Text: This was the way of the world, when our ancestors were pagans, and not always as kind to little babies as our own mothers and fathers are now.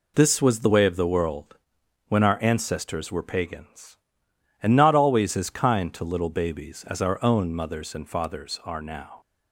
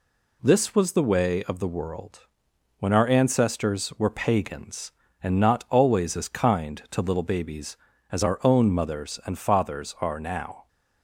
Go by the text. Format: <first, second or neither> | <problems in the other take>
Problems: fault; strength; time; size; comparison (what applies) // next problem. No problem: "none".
neither | none